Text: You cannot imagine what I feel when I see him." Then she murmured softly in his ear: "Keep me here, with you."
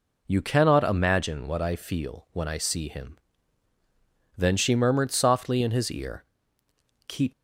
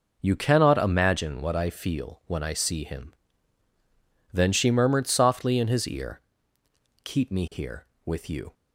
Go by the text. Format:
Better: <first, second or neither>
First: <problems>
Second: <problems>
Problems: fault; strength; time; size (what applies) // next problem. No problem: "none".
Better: second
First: stops before "me here with you"; at 7.3 s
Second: none